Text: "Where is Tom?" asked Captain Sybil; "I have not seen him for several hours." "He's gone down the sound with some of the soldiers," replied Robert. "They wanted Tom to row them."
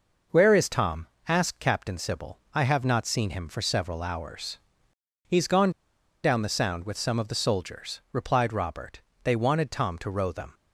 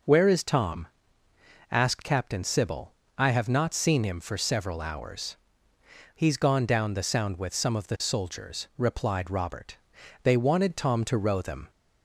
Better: second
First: pauses between "gone" and "down"; noticeable; at 5.7 s; 0.51 s long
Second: none

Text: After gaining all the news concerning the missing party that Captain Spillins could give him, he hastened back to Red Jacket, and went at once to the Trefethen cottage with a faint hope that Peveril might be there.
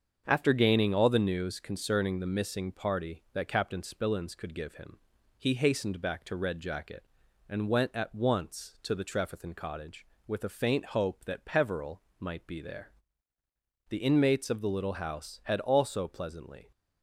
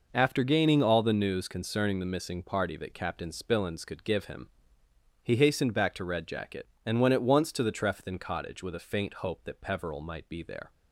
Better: second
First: starts louder than the rest; until 1.2 s; 7 dB // pauses between "Peveril" and "might"; slight; at 12.0 s; 0.18 s long // goes on to say "The inmates of the little house had also pleasantly"; strong; from 13.8 s on; 2.8 s long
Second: none

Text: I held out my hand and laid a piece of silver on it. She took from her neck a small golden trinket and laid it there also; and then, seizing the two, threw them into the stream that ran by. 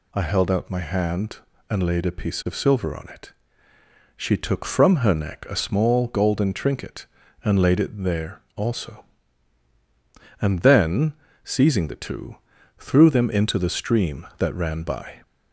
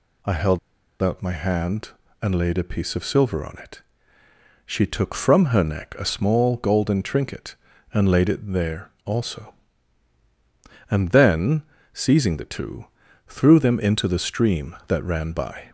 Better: first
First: none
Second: pauses between "held" and "out"; at 0.5 s; 0.42 s long

